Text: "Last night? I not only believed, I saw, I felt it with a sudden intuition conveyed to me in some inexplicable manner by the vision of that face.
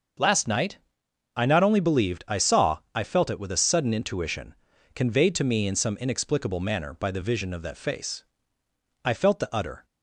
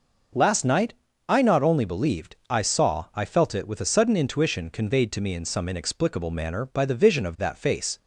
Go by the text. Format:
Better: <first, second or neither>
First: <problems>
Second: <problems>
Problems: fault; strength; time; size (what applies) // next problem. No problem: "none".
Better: second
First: starts louder than the rest; until 1.7 s; 6.5 dB // pauses between "intuition" and "conveyed"; at 4.5 s; 0.40 s long // goes on to say "I felt the utter"; noticeable; from 9.0 s on; 0.81 s long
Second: none